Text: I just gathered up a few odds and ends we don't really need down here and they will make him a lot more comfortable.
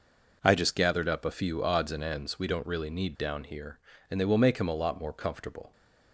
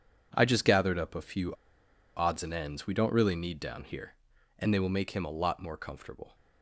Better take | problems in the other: first | pauses between "few" and "odds"; noticeable; at 1.5 s; 0.64 s long

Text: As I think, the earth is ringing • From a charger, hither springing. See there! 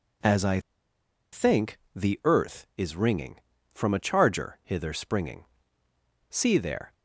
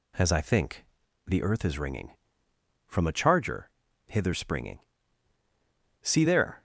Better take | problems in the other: second | pauses between "I" and "think"; noticeable; at 0.5 s; 0.72 s long

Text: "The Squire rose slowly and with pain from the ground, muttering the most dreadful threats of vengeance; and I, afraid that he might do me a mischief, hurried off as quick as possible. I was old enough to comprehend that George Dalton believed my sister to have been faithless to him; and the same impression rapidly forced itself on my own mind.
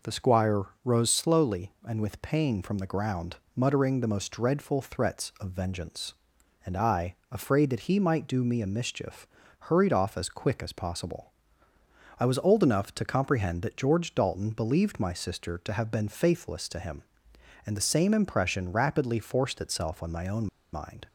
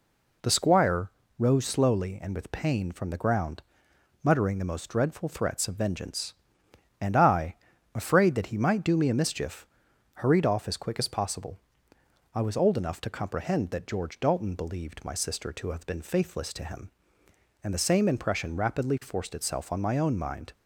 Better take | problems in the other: second | pauses between "Squire" and "rose"; slight; at 0.6 s; 0.18 s long; slight in the second // pauses between "own" and "mind"; slight; at 20.4 s; 0.25 s long

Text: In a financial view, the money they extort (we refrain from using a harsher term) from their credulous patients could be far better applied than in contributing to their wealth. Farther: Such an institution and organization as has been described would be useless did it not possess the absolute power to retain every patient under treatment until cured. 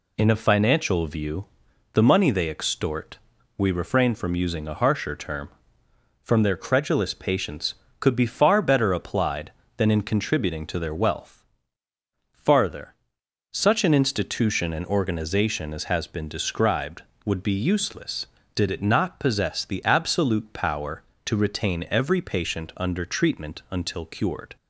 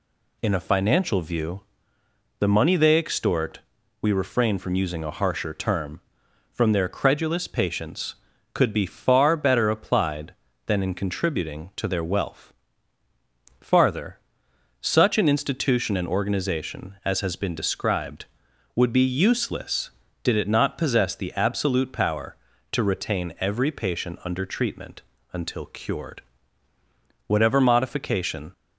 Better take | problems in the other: first | pauses between "treatment" and "until"; slight; at 25.0 s; 0.32 s long // goes on to say "Whatever modification"; noticeable; from 27.2 s on; 1.2 s long

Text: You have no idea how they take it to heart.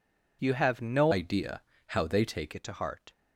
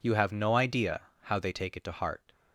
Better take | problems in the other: second | changes voice from "idea" to "take"; from 1.1 to 2.5 s; 1.4 s long // pauses between "idea" and "how"; slight; at 1.6 s; 0.28 s long; slight in the second

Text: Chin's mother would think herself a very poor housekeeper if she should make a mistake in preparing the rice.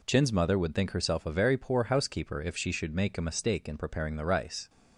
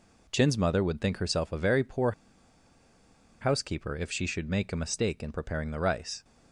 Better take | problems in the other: first | pauses between "poor" and "housekeeper"; strong; at 2.1 s; 1.2 s long

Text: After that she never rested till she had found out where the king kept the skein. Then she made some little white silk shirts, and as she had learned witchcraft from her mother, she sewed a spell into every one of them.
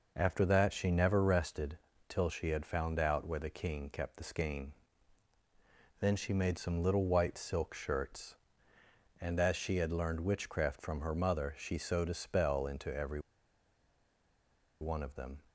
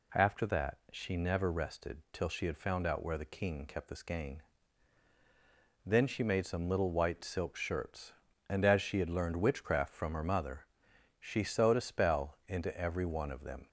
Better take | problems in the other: second | pauses between "rested" and "till"; slight; at 1.7 s; 0.30 s long // pauses between "every" and "one"; strong; at 13.2 s; 1.5 s long

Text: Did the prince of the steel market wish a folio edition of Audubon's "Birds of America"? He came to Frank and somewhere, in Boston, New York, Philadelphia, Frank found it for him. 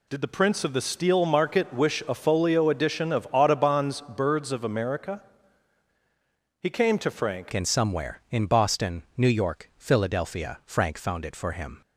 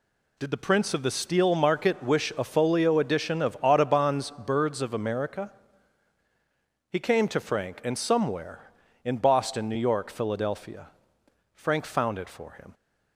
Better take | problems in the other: second | changes voice at "and"; from 7.5 s on; 4.3 s long

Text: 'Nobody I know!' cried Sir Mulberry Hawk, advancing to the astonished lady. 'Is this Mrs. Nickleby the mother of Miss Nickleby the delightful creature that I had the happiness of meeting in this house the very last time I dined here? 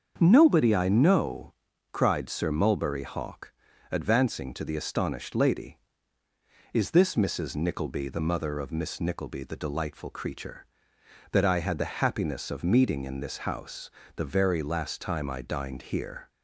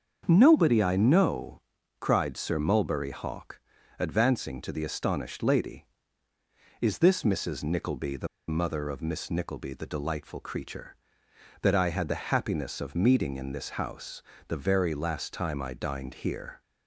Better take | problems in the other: first | starts louder than the rest; until 1.2 s; 7 dB; also in the first // pauses between "the" and "mother"; slight; at 8.2 s; 0.21 s long // pauses between "house" and "the"; slight; at 14.2 s; 0.26 s long; slight in the first

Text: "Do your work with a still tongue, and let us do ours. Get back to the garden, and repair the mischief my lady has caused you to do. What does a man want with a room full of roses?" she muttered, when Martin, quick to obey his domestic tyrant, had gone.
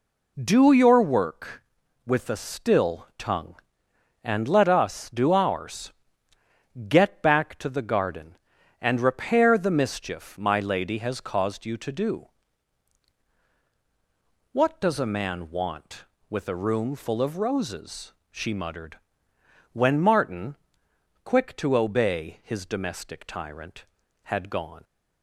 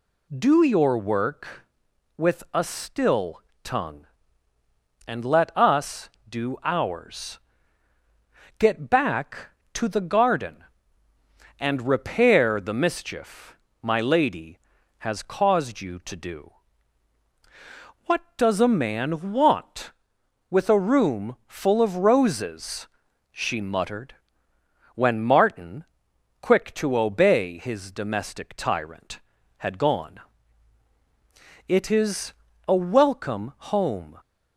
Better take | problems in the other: first | pauses between "still" and "tongue"; slight; at 3.3 s; 0.24 s long // pauses between "mischief" and "my"; slight; at 13.5 s; 0.26 s long // goes on to say "It is a welcome home"; strong; from 31.6 s on; 2.5 s long

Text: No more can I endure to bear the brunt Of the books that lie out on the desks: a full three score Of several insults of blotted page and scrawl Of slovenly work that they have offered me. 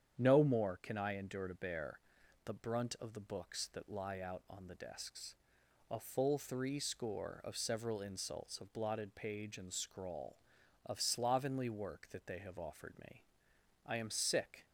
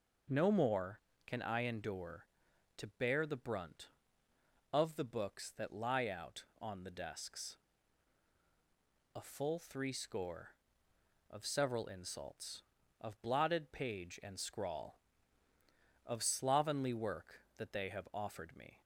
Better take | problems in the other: second | starts louder than the rest; strong; until 1.1 s; 8.5 dB // pauses between "bear" and "the"; noticeable; at 1.9 s; 0.46 s long // goes on to say "I am sick"; noticeable; from 13.8 s on; 0.80 s long

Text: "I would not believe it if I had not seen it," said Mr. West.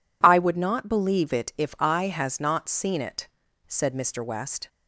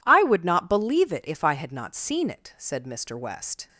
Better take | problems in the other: second | says "has" for "had"; at 2.0 s

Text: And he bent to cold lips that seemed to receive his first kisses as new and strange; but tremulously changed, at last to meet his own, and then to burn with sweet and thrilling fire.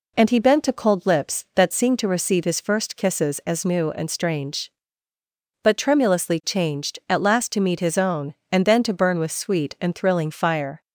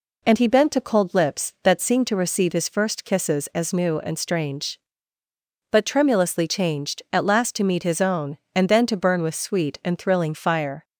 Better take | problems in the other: neither | none

